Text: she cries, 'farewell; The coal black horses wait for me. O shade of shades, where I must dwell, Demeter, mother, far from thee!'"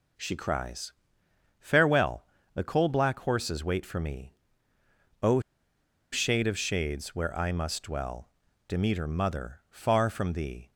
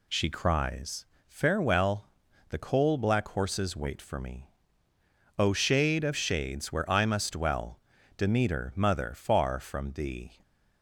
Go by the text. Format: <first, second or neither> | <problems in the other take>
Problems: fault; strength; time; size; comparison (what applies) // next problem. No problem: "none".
second | pauses between "O" and "shade"; noticeable; at 5.3 s; 0.73 s long